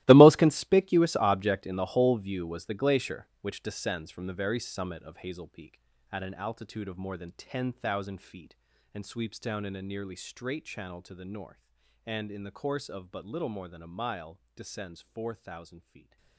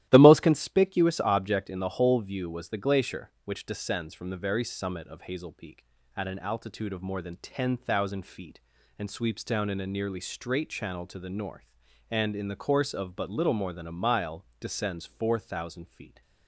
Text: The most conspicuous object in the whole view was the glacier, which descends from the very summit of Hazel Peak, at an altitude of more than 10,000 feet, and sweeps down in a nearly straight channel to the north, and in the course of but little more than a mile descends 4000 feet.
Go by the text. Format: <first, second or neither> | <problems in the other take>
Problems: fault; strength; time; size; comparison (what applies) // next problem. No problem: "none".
second | gets quieter; strong; throughout; 16.5 dB // starts louder than the rest; strong; until 1.0 s; 17 dB; strong in the second // pauses between "mile" and "descends"; slight; at 14.4 s; 0.16 s long; slight in the second